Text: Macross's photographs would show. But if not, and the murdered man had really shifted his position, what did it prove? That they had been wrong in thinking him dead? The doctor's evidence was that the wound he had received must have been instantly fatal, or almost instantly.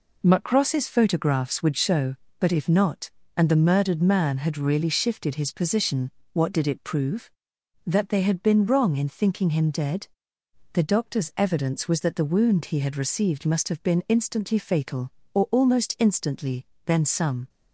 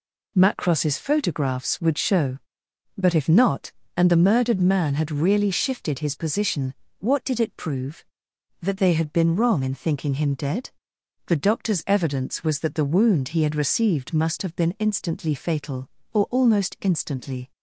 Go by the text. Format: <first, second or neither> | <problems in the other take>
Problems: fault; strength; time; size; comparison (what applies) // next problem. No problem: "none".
second | goes on to say "Then some"; noticeable; from 16.8 s on; 0.64 s long